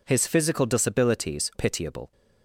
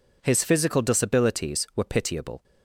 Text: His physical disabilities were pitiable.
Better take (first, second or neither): second